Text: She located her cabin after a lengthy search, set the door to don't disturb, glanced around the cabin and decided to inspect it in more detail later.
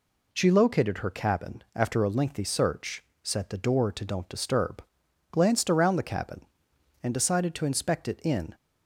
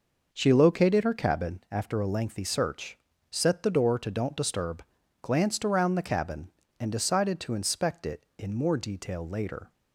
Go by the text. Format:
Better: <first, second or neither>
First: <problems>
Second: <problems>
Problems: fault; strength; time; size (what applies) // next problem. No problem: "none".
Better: second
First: stops before "more detail later"; at 8.5 s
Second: none